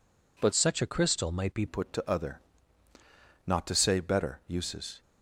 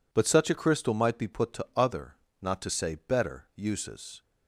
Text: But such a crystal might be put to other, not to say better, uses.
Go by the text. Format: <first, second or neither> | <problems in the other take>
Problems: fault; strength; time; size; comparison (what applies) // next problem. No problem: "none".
second | changes voice from "such" to "be"; from 0.5 to 1.6 s; 1.1 s long